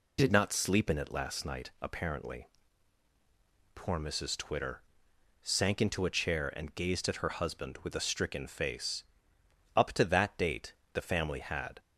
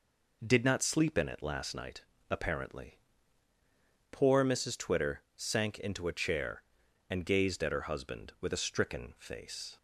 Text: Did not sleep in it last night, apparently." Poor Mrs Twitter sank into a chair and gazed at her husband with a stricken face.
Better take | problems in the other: second | pauses between "Twitter" and "sank"; noticeable; at 4.8 s; 0.60 s long // goes on to say "Up to that date the family had"; strong; from 9.7 s on; 2.0 s long

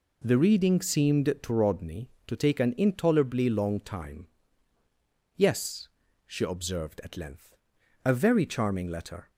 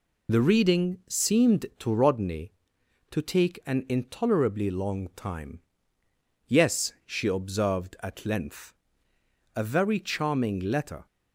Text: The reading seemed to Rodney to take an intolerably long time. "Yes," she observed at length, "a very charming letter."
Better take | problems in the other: first | loses the start of "The"; at 0.2 s; 35 ms

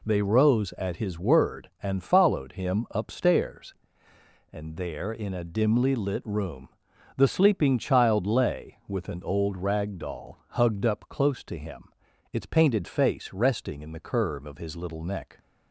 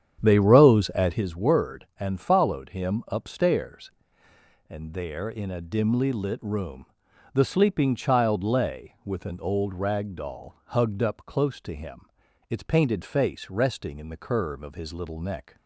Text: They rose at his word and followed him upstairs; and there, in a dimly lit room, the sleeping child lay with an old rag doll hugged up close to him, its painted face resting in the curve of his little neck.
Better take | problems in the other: first | starts louder than the rest; strong; until 1.3 s; 8.5 dB

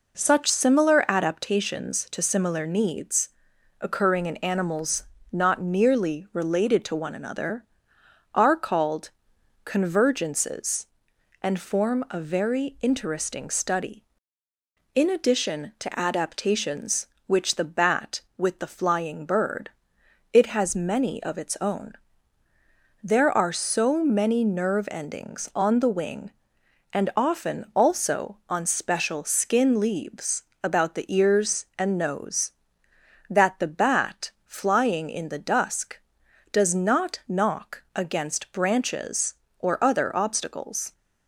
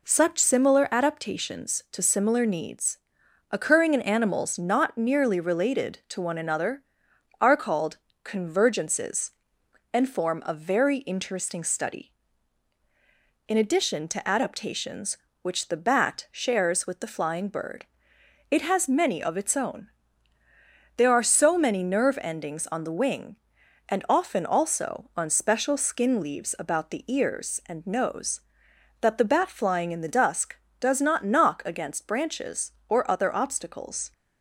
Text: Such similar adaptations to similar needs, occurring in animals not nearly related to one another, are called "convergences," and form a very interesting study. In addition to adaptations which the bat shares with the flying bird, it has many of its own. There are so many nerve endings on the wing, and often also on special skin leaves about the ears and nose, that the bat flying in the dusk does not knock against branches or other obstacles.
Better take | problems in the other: second | pauses between "animals" and "not"; slight; at 5.0 s; 0.26 s long // pauses between "called" and "convergences"; noticeable; at 9.0 s; 0.56 s long; slight in the second // skips "shares"; at 18.2 s // pauses between "leaves" and "about"; slight; at 30.4 s; 0.20 s long // pauses between "bat" and "flying"; slight; at 34.2 s; 0.16 s long

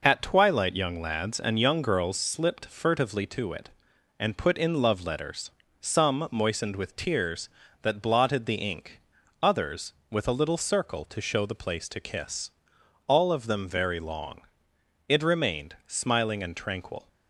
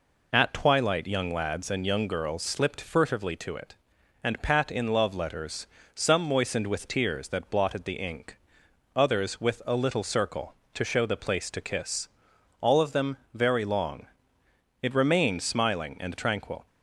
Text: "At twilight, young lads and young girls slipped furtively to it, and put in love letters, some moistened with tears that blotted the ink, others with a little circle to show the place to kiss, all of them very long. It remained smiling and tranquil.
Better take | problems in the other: first | says "pat" for "put"; at 4.4 s // pauses between "them" and "very"; slight; at 13.1 s; 0.16 s long

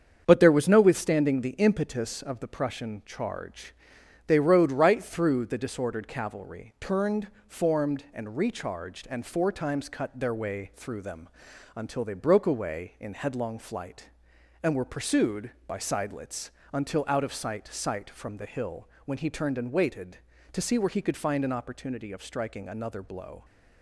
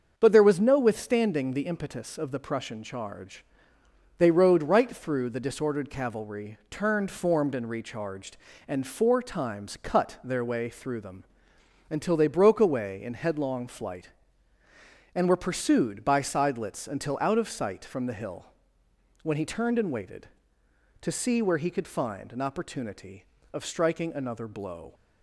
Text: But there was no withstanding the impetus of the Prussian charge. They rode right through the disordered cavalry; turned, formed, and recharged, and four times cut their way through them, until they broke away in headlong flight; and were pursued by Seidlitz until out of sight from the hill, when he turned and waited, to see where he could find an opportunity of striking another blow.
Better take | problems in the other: second | starts louder than the rest; strong; until 1.2 s; 7.5 dB; also in the second // pauses between "Seidlitz" and "until"; slight; at 16.4 s; 0.24 s long // says "sight" twice; at 17.6 s

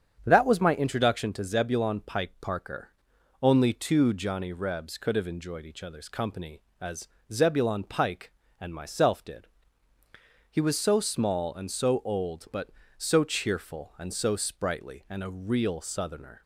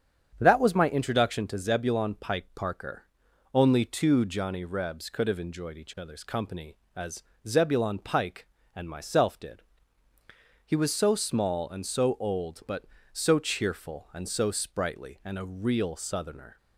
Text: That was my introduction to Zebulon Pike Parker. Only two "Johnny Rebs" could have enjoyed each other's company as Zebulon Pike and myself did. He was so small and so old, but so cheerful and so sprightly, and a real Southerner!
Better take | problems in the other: neither | starts louder than the rest; strong; the same in both // pauses between "as" and "Zebulon"; slight; the same in both

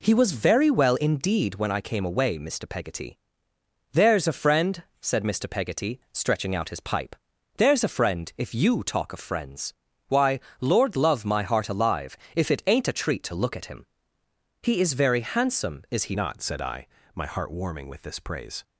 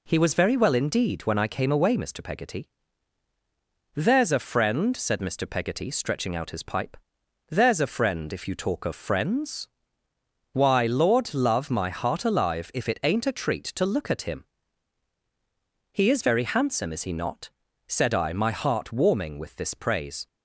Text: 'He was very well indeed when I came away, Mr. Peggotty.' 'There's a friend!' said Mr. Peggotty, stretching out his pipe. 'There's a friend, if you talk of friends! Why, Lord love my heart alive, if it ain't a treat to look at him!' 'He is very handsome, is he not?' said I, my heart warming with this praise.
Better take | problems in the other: second | changes voice at "not"; from 16.1 s on; 2.5 s long

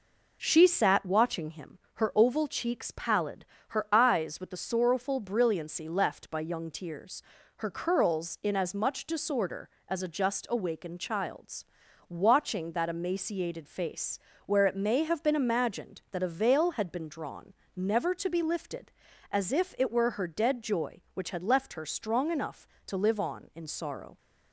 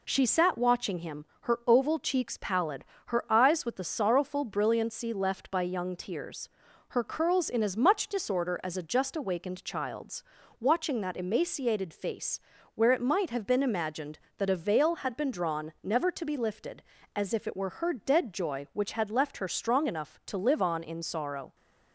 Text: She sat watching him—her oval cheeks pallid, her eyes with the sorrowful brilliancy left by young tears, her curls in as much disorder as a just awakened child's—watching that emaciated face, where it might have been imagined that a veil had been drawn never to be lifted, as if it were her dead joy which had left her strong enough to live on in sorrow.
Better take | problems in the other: second | says "may" for "might"; at 14.7 s // pauses between "drawn" and "never"; slight; at 17.5 s; 0.24 s long

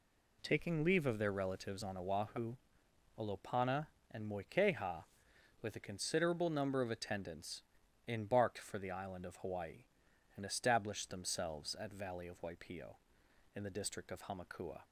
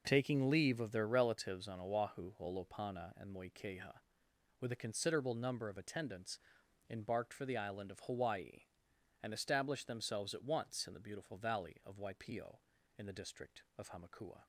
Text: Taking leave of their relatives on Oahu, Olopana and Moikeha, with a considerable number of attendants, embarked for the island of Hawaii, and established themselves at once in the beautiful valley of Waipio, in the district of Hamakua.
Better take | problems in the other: second | skips "once in the beautiful"; at 11.9 s

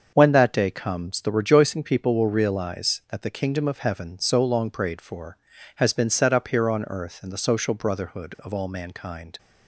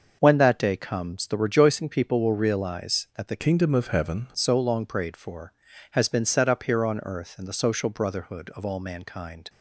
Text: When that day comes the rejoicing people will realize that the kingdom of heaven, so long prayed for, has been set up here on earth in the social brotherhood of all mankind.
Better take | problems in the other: first | starts louder than the rest; noticeable; until 1.2 s; 6 dB; also in the first // changes voice from "kingdom" to "heaven"; from 3.3 to 4.2 s; 0.9 s long

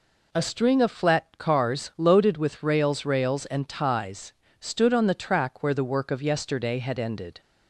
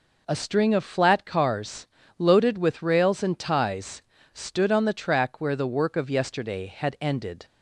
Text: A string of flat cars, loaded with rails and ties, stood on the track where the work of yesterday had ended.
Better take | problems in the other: second | says "rails" twice; at 3.0 s

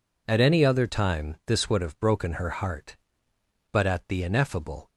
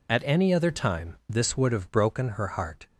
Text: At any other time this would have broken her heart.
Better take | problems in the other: second | goes on to say "But at the ineffable"; noticeable; from 3.7 s on; 1.1 s long

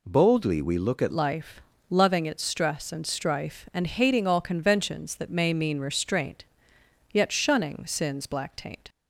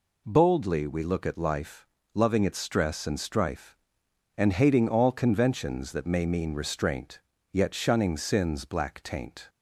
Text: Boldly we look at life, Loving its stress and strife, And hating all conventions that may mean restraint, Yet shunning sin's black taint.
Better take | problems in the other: second | changes voice at "life"; from 1.1 s on; 7.7 s long

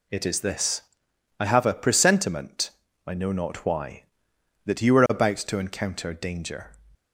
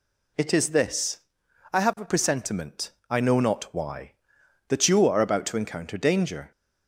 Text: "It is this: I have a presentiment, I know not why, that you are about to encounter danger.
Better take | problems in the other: neither | none

